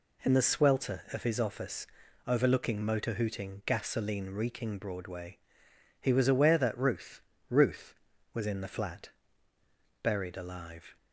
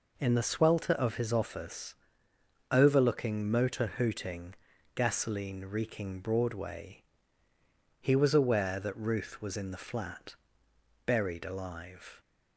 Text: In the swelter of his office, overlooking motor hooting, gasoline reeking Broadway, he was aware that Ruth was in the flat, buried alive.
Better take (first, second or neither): second